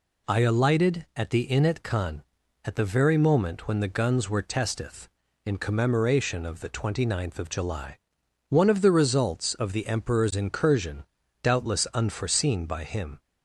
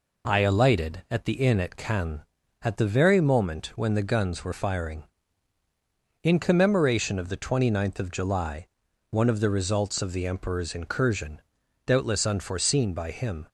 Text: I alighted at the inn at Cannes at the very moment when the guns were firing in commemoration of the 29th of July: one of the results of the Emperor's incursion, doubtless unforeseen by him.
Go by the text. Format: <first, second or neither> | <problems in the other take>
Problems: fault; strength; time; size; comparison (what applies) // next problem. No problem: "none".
second | says "testeth" for "firing"; at 4.3 s